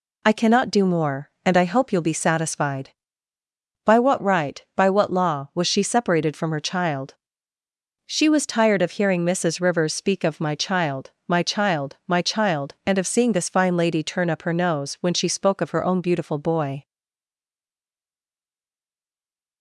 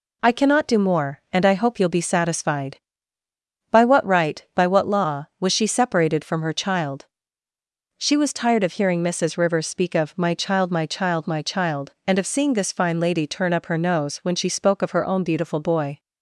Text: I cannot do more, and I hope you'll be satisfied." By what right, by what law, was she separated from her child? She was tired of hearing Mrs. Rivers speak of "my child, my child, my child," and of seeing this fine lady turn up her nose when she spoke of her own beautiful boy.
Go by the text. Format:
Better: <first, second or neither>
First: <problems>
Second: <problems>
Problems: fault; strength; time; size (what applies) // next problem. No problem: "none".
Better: second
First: stays silent after the last word; strong; from 16.8 s on; 2.8 s long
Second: none